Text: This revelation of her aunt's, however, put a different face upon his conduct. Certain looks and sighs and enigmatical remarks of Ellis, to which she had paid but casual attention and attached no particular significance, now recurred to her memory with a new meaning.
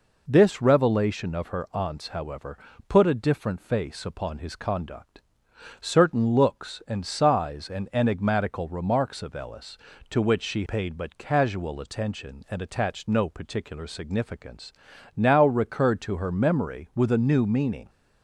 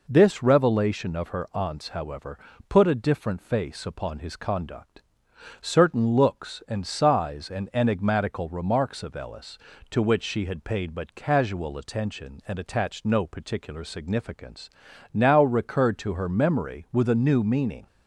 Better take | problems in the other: second | skips "had"; at 10.6 s

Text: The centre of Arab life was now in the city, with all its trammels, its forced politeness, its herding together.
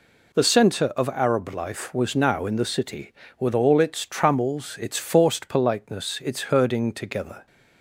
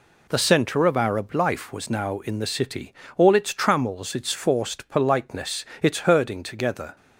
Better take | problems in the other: first | skips "with"; at 3.0 s

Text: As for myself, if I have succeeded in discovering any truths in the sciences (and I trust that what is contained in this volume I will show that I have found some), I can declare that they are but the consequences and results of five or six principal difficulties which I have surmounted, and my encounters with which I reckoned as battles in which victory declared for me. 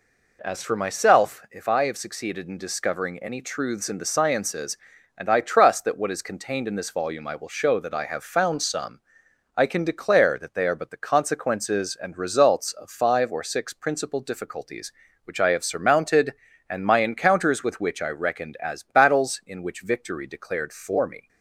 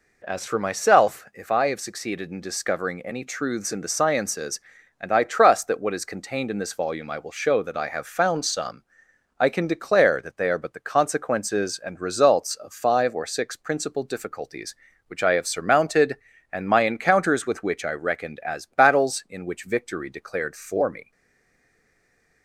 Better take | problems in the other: first | stays silent after the last word; noticeable; from 21.1 s on; 1.3 s long

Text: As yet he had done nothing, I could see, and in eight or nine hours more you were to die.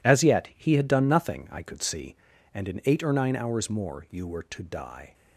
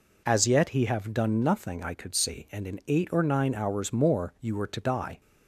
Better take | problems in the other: first | says "have" for "had"; at 0.8 s

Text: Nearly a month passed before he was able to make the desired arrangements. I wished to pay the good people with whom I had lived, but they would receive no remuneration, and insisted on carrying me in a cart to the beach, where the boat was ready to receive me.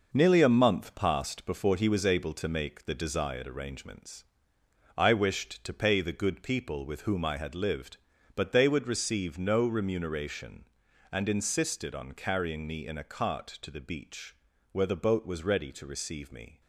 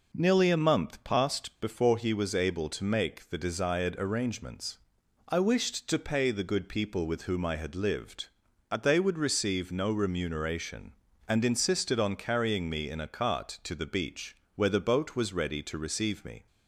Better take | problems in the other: second | gets quieter; throughout; 6.5 dB

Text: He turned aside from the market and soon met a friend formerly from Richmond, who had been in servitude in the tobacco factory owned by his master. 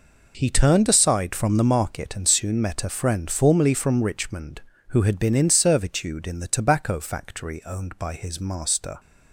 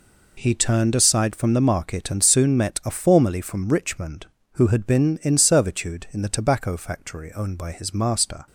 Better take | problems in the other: first | skips "friend"; at 2.9 s

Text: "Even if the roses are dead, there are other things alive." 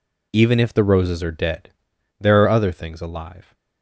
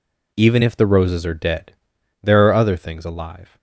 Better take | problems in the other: neither | none

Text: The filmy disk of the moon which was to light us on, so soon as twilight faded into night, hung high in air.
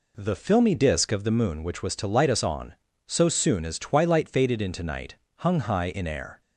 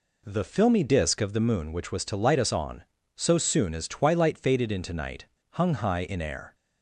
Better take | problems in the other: neither | none

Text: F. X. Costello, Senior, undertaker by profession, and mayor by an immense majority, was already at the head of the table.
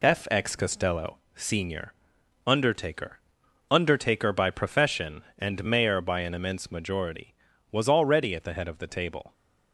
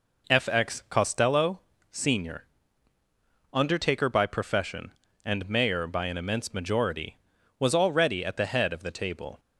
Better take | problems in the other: second | says "undertaker" twice; at 3.7 s

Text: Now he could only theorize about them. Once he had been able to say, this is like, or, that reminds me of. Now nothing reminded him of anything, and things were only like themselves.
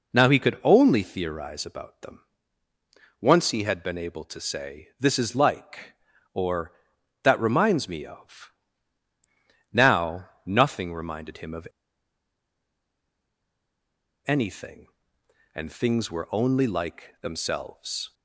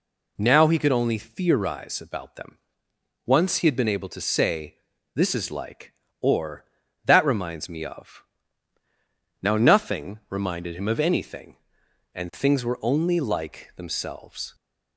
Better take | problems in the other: second | pauses between "Now" and "nothing"; slight; at 10.2 s; 0.18 s long // pauses between "of" and "anything"; strong; at 11.6 s; 2.5 s long

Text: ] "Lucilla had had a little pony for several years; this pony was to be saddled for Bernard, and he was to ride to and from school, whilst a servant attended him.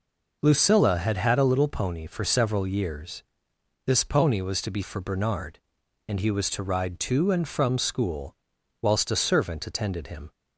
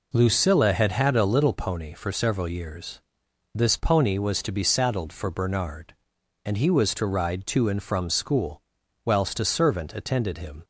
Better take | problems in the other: second | skips "saddled"; at 4.8 s

